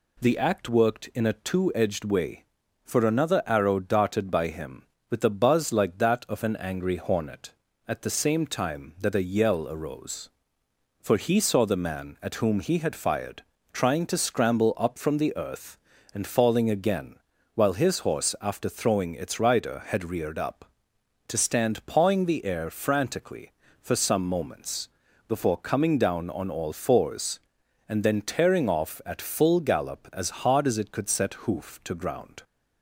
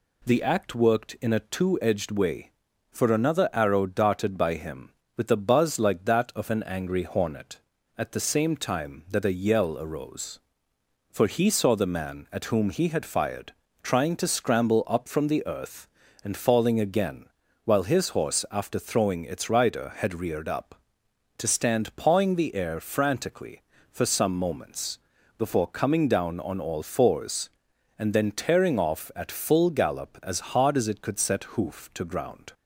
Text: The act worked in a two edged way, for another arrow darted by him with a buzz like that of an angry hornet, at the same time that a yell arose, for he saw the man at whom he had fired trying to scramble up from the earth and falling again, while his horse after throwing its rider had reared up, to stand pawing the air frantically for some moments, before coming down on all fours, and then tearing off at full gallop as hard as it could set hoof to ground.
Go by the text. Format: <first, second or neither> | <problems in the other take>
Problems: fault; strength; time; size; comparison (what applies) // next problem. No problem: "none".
neither | pauses between "fired" and "trying"; slight; the same in both